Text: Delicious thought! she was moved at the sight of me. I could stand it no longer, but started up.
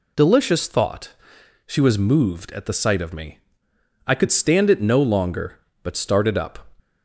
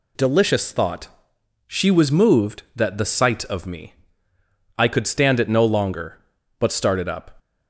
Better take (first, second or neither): first